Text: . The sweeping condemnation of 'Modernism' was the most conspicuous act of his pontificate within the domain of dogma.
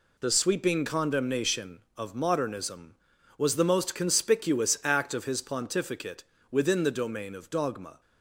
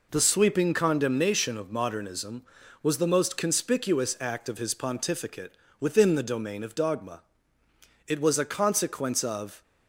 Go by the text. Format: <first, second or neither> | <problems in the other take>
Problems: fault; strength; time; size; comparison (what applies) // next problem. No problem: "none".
first | pauses between "pontificate" and "within"; slight; at 5.5 s; 0.24 s long; slight in the first // goes on to say "It was a consequence of"; from 8.0 s on; 1.5 s long